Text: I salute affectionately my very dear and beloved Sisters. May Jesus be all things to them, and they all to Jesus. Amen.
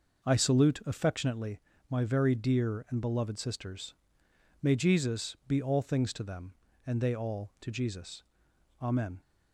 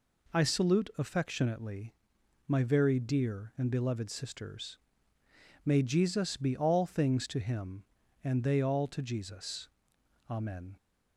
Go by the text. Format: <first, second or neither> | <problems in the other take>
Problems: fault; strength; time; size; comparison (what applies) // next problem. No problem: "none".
first | pauses between "affectionately" and "my"; noticeable; at 1.9 s; 0.54 s long; slight in the first // says "him" for "them"; at 7.3 s